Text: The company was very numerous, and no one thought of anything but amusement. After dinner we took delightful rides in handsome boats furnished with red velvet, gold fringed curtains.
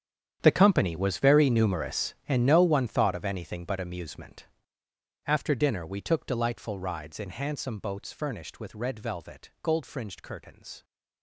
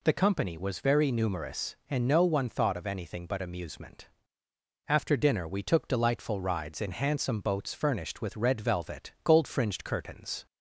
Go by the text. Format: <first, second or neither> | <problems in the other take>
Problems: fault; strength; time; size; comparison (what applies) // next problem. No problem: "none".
second | gets quieter; strong; throughout; 16 dB